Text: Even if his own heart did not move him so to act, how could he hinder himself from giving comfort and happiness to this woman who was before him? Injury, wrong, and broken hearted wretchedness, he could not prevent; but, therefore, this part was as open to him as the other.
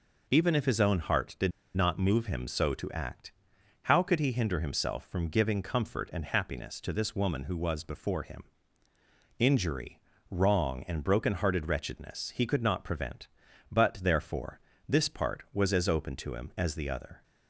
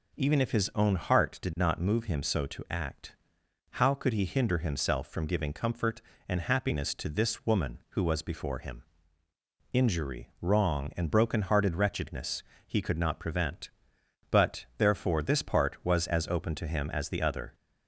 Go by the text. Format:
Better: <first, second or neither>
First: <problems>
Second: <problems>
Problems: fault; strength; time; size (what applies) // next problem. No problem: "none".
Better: second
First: pauses between "did" and "not"; slight; at 1.5 s; 0.23 s long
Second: none